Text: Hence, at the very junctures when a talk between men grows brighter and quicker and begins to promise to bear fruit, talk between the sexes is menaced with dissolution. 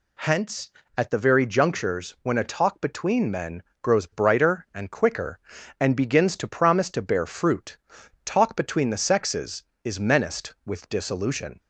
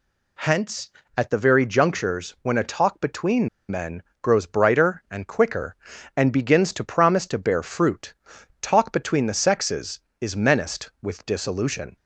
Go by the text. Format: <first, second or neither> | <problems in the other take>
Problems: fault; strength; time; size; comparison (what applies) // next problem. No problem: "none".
first | pauses between "between" and "men"; slight; at 3.4 s; 0.20 s long // pauses between "men" and "grows"; slight; at 4.0 s; 0.22 s long; slight in the first